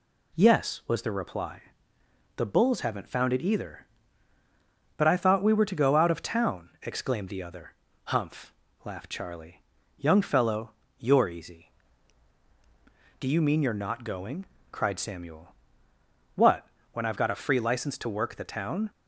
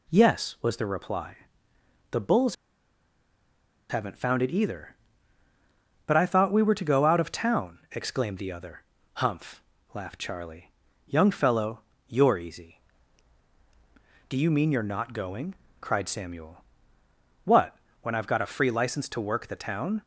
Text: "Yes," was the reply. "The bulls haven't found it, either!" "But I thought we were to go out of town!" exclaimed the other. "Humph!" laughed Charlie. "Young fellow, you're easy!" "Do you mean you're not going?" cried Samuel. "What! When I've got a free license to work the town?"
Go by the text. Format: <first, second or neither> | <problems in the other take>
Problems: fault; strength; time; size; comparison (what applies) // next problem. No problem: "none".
first | pauses between "bulls" and "haven't"; strong; at 2.5 s; 1.3 s long